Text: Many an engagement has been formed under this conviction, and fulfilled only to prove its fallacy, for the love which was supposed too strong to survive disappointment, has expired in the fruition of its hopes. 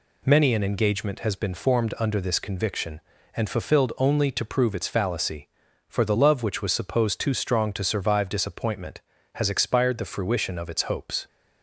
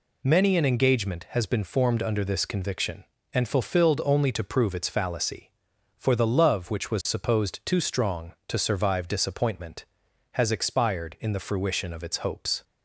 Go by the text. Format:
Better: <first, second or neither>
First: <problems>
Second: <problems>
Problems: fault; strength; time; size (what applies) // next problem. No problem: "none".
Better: second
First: skips "in"; at 9.9 s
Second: none